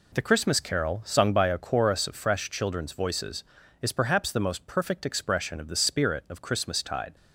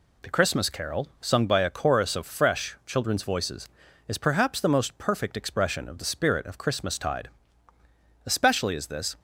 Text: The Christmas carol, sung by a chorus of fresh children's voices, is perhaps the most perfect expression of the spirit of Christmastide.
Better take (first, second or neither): first